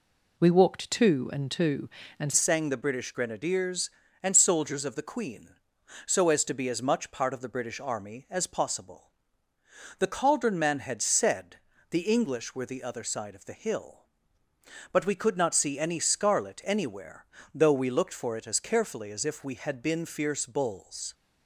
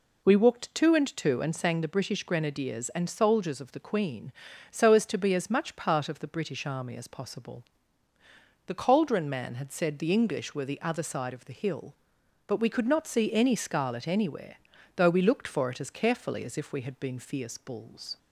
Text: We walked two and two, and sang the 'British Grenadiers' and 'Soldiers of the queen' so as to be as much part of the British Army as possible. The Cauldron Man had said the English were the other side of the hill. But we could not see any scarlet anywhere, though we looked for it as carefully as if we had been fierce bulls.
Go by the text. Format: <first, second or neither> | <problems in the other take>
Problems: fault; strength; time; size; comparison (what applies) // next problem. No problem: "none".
second | changes voice at "sang"; from 2.3 s on; 18.8 s long // pauses between "said" and "the"; slight; at 11.5 s; 0.34 s long